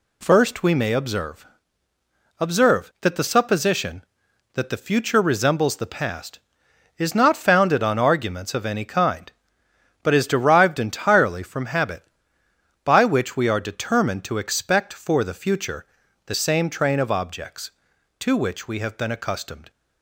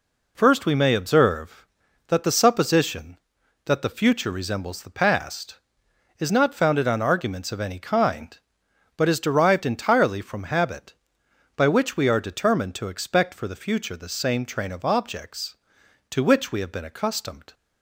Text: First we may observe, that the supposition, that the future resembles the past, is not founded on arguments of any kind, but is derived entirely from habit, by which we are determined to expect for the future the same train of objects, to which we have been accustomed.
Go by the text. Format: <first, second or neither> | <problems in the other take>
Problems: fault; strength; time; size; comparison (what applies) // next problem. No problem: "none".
second | says "observe" twice; at 2.3 s // pauses between "future" and "the"; at 15.8 s; 0.40 s long